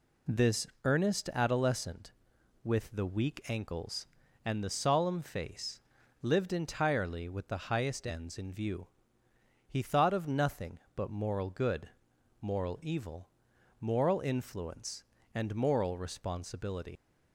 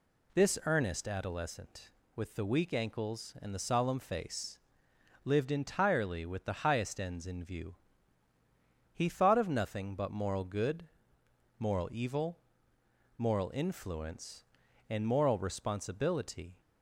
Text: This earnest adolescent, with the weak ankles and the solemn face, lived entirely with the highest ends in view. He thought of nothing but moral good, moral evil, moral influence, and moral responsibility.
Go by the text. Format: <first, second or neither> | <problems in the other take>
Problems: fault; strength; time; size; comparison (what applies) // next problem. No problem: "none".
second | pauses between "This" and "earnest"; slight; at 0.6 s; 0.16 s long // leaves "responsibility" unfinished; at 16.9 s; 105 ms